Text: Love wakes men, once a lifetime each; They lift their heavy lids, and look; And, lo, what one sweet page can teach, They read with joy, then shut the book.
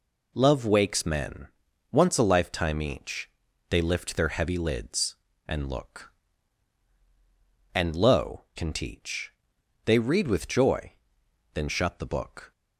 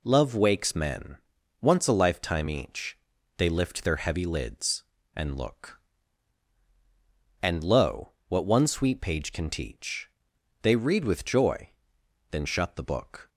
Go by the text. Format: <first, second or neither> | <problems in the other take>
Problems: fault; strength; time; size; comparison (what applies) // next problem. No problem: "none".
second | skips "what one sweet page"; at 8.5 s